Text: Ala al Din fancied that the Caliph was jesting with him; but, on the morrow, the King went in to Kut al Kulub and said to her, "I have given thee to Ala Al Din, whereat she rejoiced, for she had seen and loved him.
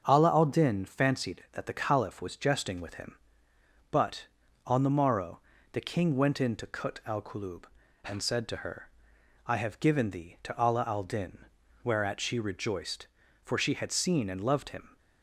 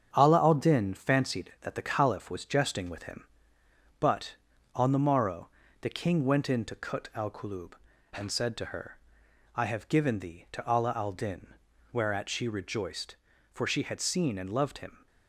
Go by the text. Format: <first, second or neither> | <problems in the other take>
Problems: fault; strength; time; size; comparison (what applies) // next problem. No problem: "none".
first | gets quieter; noticeable; throughout; 5.5 dB // starts louder than the rest; strong; until 1.1 s; 7.5 dB; also in the first